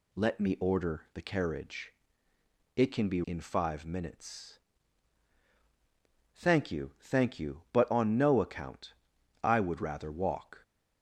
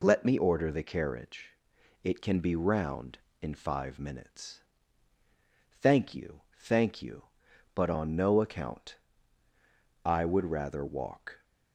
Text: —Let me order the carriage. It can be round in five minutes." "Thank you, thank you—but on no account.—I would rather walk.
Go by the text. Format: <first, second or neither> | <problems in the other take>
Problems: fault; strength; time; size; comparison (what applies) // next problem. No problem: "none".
second | skips "round"; at 3.2 s